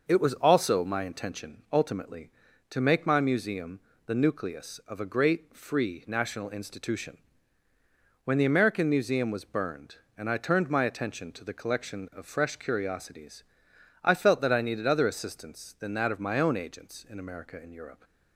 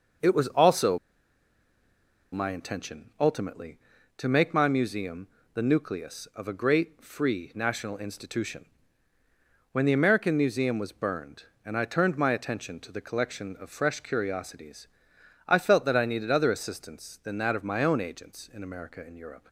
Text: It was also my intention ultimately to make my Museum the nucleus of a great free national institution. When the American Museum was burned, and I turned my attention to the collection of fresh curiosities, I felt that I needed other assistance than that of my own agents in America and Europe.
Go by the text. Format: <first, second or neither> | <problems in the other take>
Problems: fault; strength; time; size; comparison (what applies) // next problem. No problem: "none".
first | starts louder than the rest; noticeable; until 2.5 s; 6 dB; noticeable in the first // pauses between "also" and "my"; strong; at 0.9 s; 1.3 s long // pauses between "Museum" and "the"; slight; at 5.2 s; 0.26 s long; slight in the first